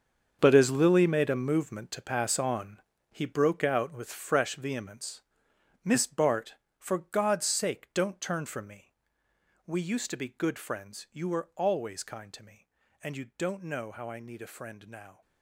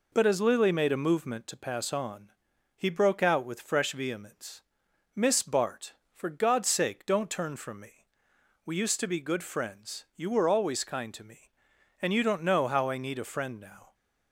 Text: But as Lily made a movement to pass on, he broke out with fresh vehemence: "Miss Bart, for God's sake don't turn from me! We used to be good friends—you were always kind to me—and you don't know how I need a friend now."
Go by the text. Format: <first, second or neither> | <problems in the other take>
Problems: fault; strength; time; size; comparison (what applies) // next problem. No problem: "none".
second | gets quieter; strong; throughout; 13.5 dB